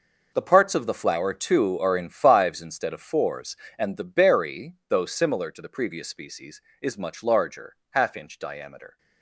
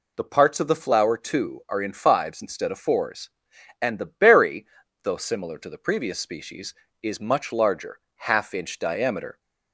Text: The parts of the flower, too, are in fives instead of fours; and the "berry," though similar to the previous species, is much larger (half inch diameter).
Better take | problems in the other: second | gets quieter; strong; throughout; 13 dB

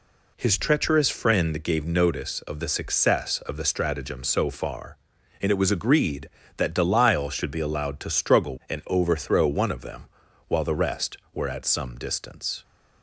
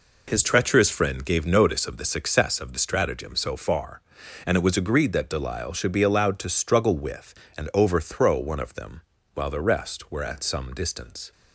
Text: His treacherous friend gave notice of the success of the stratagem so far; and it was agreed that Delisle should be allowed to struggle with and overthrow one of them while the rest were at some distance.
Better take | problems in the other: second | skips "with"; at 8.6 s // pauses between "them" and "while"; at 10.0 s; 0.42 s long; slight in the second

